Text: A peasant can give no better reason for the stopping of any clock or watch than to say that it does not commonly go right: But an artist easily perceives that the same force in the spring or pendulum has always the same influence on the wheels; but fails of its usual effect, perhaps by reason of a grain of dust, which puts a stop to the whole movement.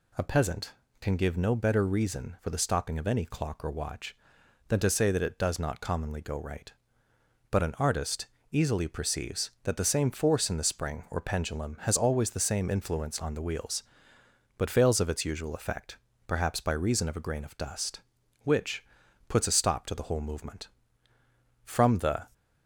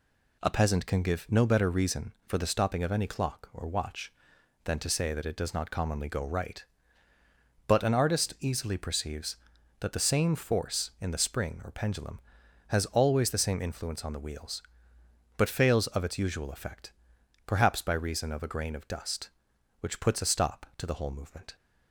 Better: second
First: pauses between "artist" and "easily"; slight; at 8.2 s; 0.24 s long // pauses between "which" and "puts"; noticeable; at 18.8 s; 0.46 s long // goes on to say "From the"; noticeable; from 21.6 s on; 0.64 s long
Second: none

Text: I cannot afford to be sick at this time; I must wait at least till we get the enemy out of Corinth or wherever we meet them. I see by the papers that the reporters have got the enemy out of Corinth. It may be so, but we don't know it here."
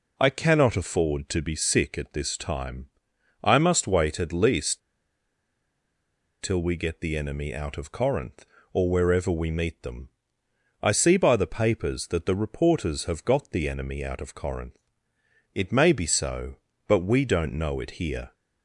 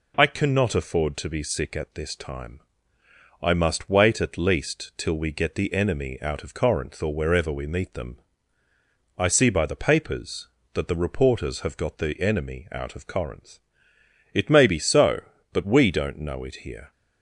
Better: second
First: pauses between "least" and "till"; strong; at 4.8 s; 1.6 s long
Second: none

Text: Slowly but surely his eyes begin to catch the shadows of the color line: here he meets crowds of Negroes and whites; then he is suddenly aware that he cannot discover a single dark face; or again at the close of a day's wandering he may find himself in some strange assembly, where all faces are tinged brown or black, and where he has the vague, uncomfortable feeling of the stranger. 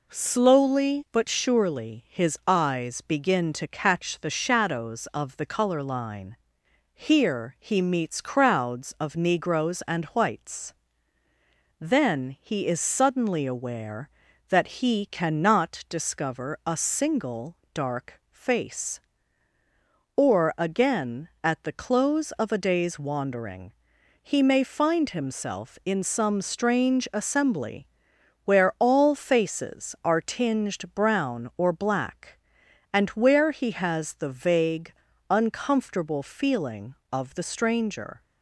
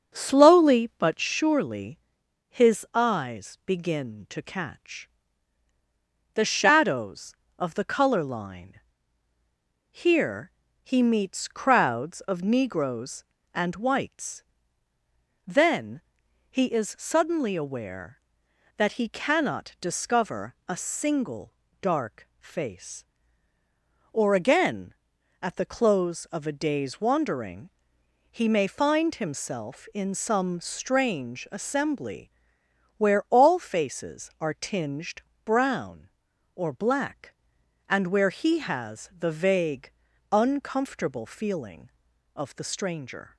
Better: first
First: pauses between "single" and "dark"; slight; at 17.5 s; 0.20 s long // pauses between "wandering" and "he"; noticeable; at 23.7 s; 0.50 s long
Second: starts louder than the rest; until 1.3 s; 6.5 dB // pauses between "surely" and "his"; noticeable; at 1.9 s; 0.50 s long // pauses between "catch" and "the"; strong; at 5.0 s; 1.2 s long // pauses between "here" and "he"; slight; at 10.5 s; 0.32 s long // pauses between "then" and "he"; noticeable; at 15.9 s; 0.52 s long // pauses between "single" and "dark"; slight; at 21.5 s; 0.28 s long // pauses between "wandering" and "he"; noticeable; at 27.7 s; 0.64 s long // pauses between "tinged" and "brown"; slight; at 35.2 s; 0.24 s long

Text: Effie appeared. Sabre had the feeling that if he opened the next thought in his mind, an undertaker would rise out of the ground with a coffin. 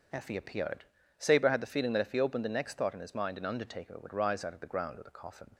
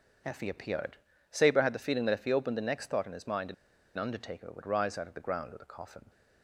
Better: first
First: starts louder than the rest; until 1.4 s; 7 dB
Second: starts louder than the rest; until 1.6 s; 7 dB // pauses between "an" and "undertaker"; at 3.5 s; 0.42 s long

